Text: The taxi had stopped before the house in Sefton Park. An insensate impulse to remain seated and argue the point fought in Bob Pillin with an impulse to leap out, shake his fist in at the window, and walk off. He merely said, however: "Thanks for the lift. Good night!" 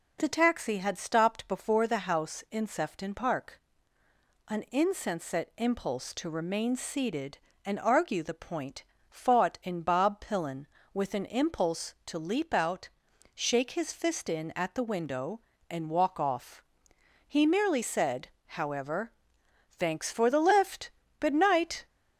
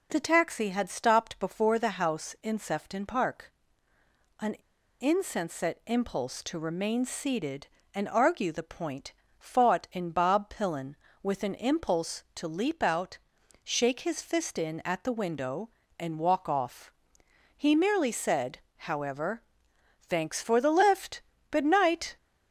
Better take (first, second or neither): first